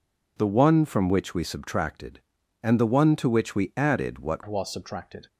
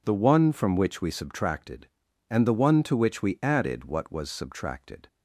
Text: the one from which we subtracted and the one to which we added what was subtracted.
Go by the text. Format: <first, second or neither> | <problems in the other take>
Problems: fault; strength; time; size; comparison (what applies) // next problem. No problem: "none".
second | changes voice at "was"; from 4.4 s on; 0.8 s long